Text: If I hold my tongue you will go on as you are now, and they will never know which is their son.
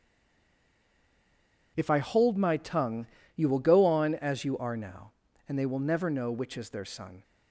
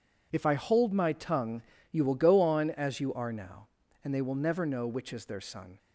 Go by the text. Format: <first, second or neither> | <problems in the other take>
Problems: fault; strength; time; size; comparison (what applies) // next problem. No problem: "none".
second | stays silent before the first word; noticeable; until 1.7 s; 1.7 s long // pauses between "tongue" and "you"; slight; at 3.0 s; 0.28 s long; slight in the second